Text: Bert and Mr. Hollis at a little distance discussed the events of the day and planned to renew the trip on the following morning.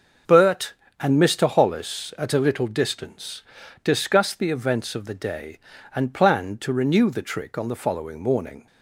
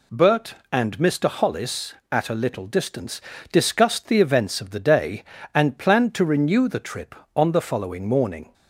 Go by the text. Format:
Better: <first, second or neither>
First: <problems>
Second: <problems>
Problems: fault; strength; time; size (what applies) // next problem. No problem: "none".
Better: second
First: starts louder than the rest; until 1.4 s; 6 dB // pauses between "distance" and "discussed"; at 3.4 s; 0.42 s long // says "trick" for "trip"; at 7.2 s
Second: pauses between "distance" and "discussed"; slight; at 3.2 s; 0.30 s long